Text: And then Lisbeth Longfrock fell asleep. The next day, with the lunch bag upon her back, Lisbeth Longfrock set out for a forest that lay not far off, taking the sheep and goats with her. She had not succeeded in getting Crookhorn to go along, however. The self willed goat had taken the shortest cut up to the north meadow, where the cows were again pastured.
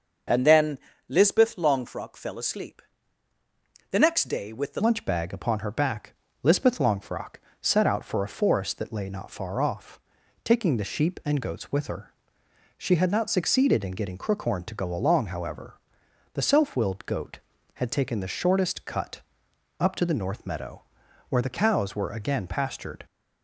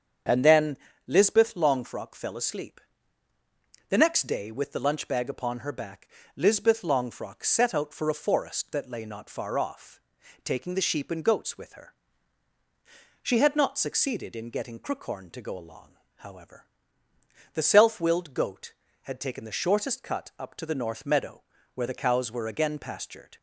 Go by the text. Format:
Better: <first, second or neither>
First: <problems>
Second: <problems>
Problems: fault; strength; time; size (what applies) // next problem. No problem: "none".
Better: second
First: starts louder than the rest; until 1.5 s; 6 dB // pauses between "then" and "Lisbeth"; slight; at 0.7 s; 0.30 s long // changes voice at "lunch"; from 4.7 s on; 18.3 s long // pauses between "Longfrock" and "set"; slight; at 7.3 s; 0.26 s long // pauses between "cut" and "up"; noticeable; at 19.2 s; 0.58 s long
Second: starts louder than the rest; strong; until 1.5 s; 7 dB // pauses between "then" and "Lisbeth"; slight; at 0.7 s; 0.30 s long